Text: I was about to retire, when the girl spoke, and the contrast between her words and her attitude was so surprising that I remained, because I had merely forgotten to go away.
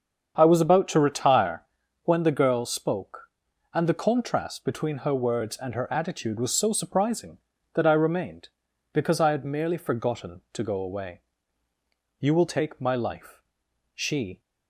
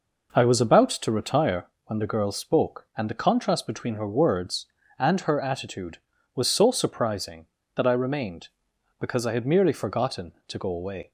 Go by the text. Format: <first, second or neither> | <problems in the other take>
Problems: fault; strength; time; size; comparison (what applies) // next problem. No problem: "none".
second | starts louder than the rest; strong; until 1.3 s; 7.5 dB // goes on to say "You will take my life she"; strong; from 12.2 s on; 2.2 s long